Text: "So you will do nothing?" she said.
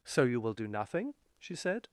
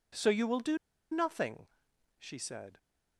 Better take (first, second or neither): first